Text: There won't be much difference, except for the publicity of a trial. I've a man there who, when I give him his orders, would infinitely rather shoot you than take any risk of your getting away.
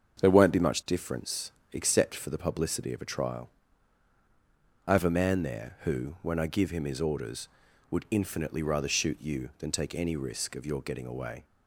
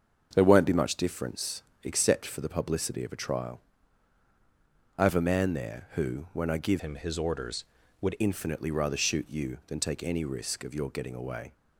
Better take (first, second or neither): first